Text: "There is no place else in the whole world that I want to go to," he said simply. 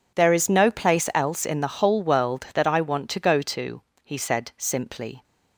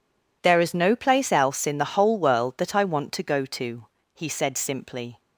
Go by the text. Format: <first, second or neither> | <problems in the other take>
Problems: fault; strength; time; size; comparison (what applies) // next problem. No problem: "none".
neither | none